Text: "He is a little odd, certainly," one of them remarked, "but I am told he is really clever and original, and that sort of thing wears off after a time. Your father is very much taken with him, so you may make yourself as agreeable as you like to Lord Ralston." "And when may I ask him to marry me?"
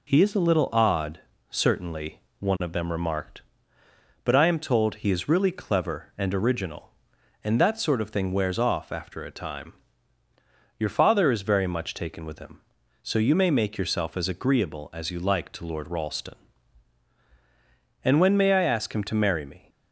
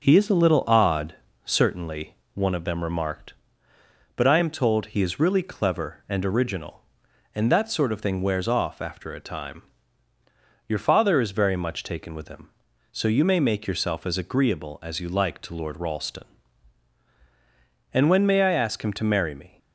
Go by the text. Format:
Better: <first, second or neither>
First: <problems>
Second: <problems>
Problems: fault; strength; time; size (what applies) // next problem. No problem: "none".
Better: first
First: none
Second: starts louder than the rest; noticeable; until 1.7 s; 5.5 dB